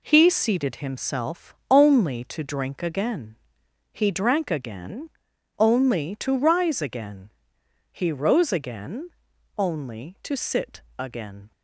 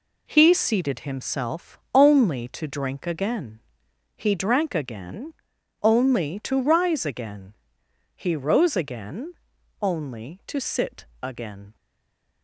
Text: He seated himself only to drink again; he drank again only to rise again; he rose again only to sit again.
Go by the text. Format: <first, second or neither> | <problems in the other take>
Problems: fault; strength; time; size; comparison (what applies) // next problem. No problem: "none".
first | pauses between "again" and "only"; noticeable; at 5.3 s; 0.48 s long; noticeable in the first // pauses between "again" and "only"; noticeable; at 9.3 s; 0.46 s long; noticeable in the first // pauses between "sit" and "again"; slight; at 11.0 s; 0.18 s long; slight in the first // stays silent after the last word; slight; from 11.7 s on; 0.7 s long